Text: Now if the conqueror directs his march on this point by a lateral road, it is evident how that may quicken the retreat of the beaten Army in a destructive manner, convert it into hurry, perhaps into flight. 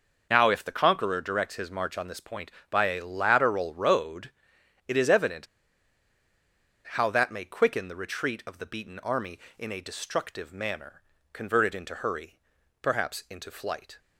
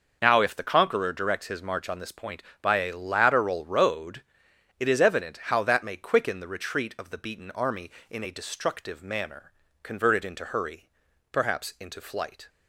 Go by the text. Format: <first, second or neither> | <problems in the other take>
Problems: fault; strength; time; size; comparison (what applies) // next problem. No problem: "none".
second | pauses between "evident" and "how"; strong; at 5.4 s; 1.4 s long